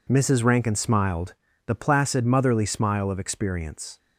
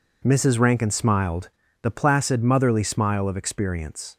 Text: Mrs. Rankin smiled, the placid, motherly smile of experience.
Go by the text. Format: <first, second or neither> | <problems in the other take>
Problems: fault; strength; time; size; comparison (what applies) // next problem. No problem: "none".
neither | none